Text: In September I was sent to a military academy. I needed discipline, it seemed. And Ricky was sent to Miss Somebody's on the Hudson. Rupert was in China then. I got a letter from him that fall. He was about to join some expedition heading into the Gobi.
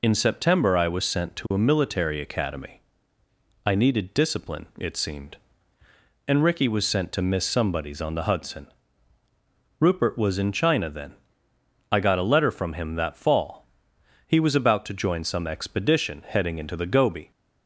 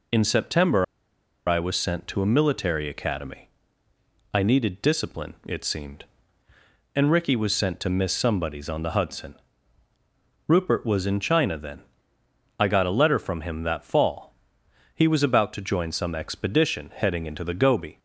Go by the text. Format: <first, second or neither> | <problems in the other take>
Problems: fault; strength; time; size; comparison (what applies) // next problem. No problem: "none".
first | pauses between "September" and "I"; noticeable; at 0.8 s; 0.63 s long